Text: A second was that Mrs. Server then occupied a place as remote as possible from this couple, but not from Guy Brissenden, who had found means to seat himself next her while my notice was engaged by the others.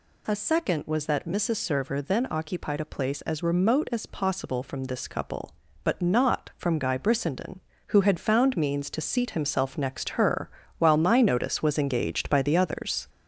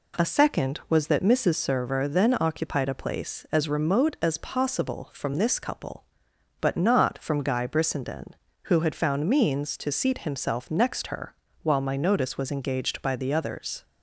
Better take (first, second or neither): second